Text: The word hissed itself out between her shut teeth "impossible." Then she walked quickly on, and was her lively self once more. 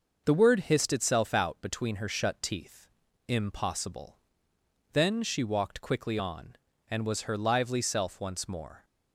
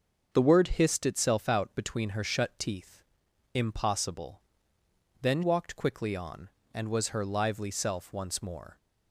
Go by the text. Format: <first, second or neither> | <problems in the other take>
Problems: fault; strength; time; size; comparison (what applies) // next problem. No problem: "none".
first | starts louder than the rest; until 1.3 s; 7 dB; noticeable in the first // pauses between "teeth" and "impossible"; noticeable; at 3.0 s; 0.54 s long; also in the first // skips "she"; at 5.4 s